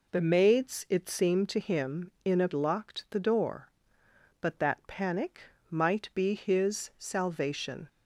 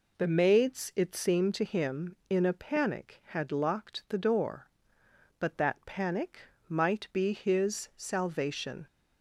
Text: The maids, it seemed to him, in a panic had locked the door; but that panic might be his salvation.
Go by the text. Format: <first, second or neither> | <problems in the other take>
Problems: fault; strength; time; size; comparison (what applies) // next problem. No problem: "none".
second | skips "panic had"; at 2.5 s // pauses between "panic" and "might"; slight; at 5.4 s; 0.28 s long; slight in the second